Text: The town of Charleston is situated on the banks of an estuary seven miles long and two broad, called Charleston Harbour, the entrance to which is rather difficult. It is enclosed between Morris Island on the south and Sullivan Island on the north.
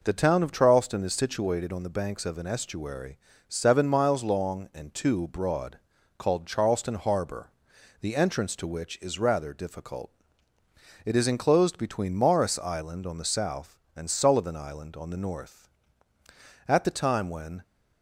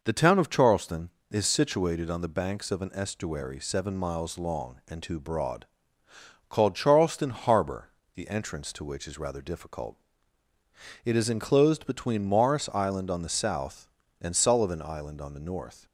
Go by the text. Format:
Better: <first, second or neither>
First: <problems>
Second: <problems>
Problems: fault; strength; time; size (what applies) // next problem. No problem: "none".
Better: second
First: pauses between "estuary" and "seven"; slight; at 3.1 s; 0.30 s long // goes on to say "At the time when"; noticeable; from 16.6 s on; 0.94 s long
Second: none